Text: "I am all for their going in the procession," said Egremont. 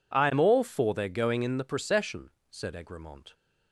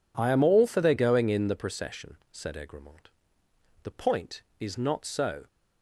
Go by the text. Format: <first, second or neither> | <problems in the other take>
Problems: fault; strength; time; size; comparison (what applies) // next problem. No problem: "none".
first | goes on to say "The point is not so"; from 3.8 s on; 1.6 s long